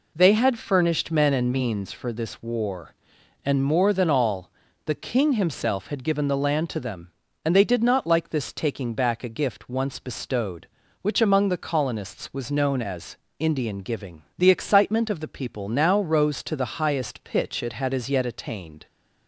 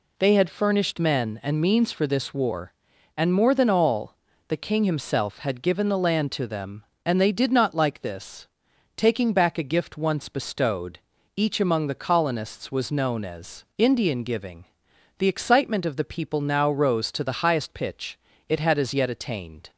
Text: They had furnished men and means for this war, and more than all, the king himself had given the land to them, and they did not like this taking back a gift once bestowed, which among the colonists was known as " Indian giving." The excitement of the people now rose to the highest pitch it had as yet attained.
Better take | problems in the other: first | pauses between "this" and "taking"; noticeable; at 8.4 s; 0.48 s long // says "each" for "which"; at 11.3 s // pauses between "pitch" and "it"; slight; at 18.1 s; 0.30 s long

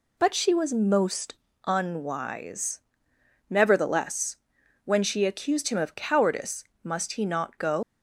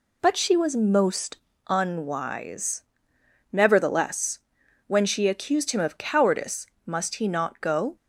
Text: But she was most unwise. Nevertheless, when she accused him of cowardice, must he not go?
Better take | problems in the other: second | pauses between "most" and "unwise"; slight; at 1.3 s; 0.30 s long; slight in the second // leaves "go" unfinished; at 7.8 s; 100 ms

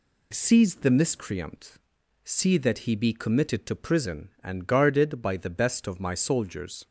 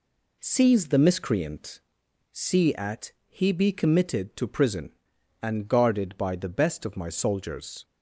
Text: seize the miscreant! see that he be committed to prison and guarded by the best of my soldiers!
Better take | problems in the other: first | says "at" for "that"; at 2.7 s

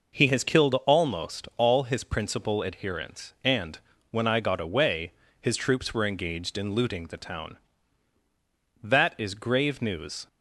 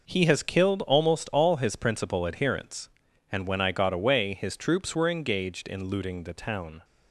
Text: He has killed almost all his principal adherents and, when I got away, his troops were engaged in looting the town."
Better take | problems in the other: second | goes on to say "That is grave news"; from 8.7 s on; 1.4 s long

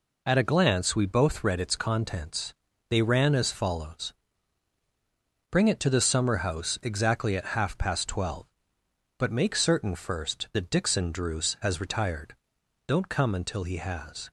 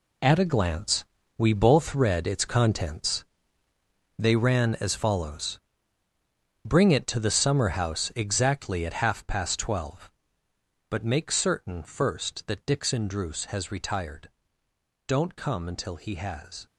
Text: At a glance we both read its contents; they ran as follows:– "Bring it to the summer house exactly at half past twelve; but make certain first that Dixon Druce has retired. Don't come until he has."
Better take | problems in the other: first | gets quieter; strong; throughout; 11.5 dB // pauses between "glance" and "we"; slight; at 1.0 s; 0.34 s long

